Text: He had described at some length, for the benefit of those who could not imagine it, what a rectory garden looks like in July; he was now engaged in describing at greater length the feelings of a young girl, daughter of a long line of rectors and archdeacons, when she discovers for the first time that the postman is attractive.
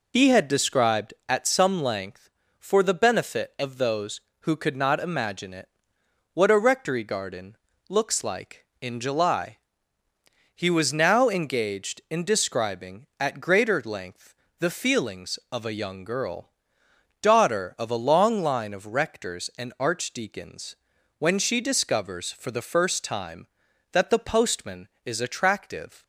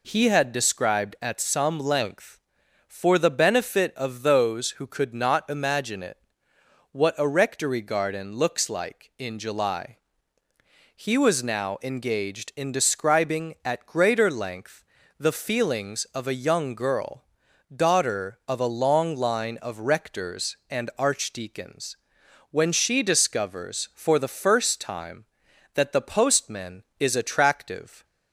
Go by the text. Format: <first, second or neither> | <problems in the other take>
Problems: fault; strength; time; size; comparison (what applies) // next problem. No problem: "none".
second | loses the start of "He"; at 0.1 s; 65 ms // pauses between "garden" and "looks"; slight; at 7.5 s; 0.34 s long // pauses between "length" and "the"; slight; at 14.3 s; 0.28 s long; slight in the second